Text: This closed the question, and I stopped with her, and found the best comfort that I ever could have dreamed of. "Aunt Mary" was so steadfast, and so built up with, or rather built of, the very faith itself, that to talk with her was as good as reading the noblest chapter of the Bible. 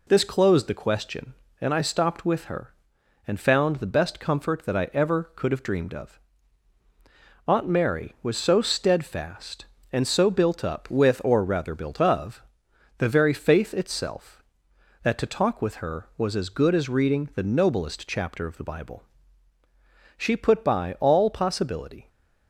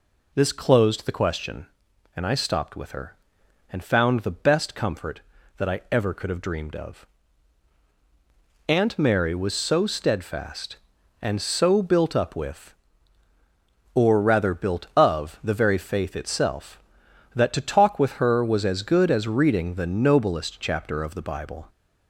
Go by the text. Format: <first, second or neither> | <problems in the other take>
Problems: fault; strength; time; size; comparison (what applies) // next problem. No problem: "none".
second | goes on to say "She put by all possibility"; strong; from 20.1 s on; 1.9 s long